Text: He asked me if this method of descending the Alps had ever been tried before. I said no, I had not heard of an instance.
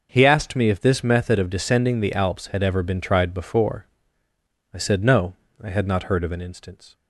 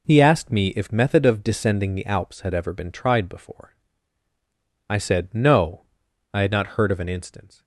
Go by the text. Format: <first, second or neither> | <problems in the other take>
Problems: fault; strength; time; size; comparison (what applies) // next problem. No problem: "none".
first | skips "this"; at 0.9 s